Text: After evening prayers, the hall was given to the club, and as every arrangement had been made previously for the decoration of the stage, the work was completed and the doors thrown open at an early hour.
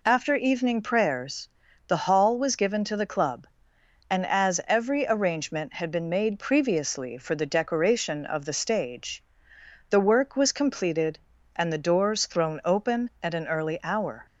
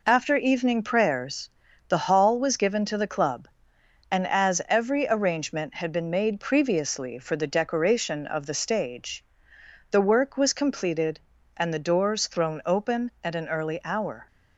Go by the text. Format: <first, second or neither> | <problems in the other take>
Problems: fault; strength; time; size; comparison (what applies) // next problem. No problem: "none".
first | gets quieter; noticeable; throughout; 5.5 dB